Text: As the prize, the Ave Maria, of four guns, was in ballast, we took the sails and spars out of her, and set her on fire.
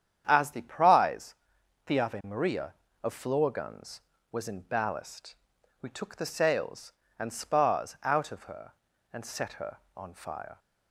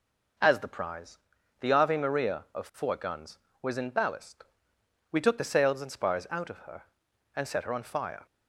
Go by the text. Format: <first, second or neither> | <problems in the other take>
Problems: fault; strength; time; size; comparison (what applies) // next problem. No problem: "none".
second | starts louder than the rest; strong; until 1.2 s; 9 dB // says "floor" for "four"; at 3.1 s